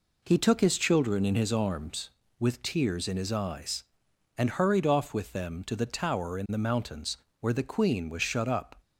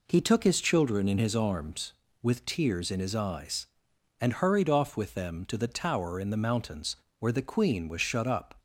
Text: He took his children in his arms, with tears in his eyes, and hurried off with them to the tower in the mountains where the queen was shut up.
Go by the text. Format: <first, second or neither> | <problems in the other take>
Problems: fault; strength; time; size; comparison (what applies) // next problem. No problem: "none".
neither | pauses between "mountains" and "where"; slight; the same in both